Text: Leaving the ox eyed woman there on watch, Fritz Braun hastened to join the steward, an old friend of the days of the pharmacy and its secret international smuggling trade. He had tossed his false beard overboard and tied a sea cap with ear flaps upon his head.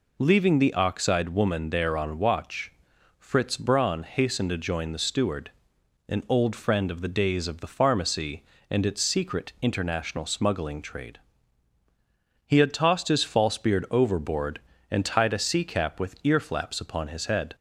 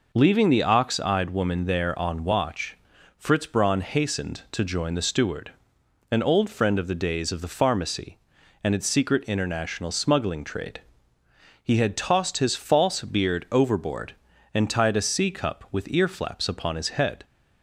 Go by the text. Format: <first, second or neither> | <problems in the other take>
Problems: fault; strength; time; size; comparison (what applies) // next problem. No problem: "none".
first | says "cup" for "cap"; at 15.3 s